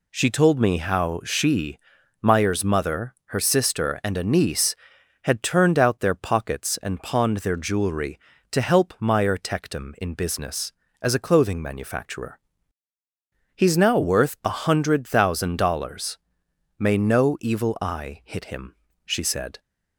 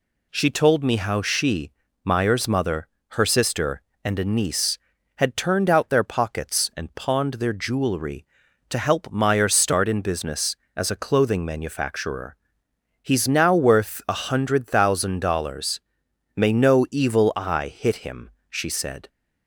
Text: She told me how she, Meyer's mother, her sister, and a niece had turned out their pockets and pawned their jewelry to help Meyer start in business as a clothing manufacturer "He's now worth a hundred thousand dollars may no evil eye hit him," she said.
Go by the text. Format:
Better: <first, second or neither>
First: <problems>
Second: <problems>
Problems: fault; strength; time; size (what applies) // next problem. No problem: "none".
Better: second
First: says "tectum" for "start"; at 9.3 s // pauses between "manufacturer" and "He's"; at 12.3 s; 1.1 s long // pauses between "dollars" and "may"; noticeable; at 16.1 s; 0.62 s long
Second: pauses between "manufacturer" and "He's"; noticeable; at 12.3 s; 0.64 s long // pauses between "dollars" and "may"; noticeable; at 15.8 s; 0.56 s long